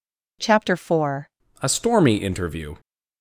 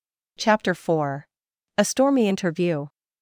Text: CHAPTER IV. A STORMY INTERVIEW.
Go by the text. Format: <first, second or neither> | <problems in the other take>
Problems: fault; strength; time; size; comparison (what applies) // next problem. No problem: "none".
second | changes voice at "A"; from 1.6 s on; 1.1 s long